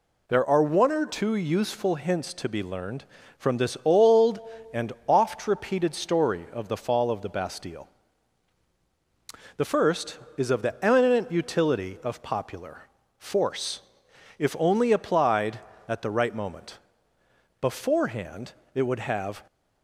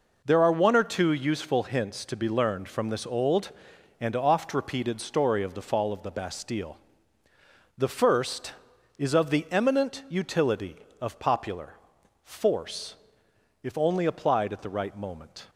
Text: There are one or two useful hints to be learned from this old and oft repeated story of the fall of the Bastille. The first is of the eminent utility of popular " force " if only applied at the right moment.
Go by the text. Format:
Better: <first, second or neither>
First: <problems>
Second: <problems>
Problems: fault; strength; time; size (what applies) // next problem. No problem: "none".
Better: second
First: goes on to say "Beforehand it would have"; strong; from 17.6 s on; 1.8 s long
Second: none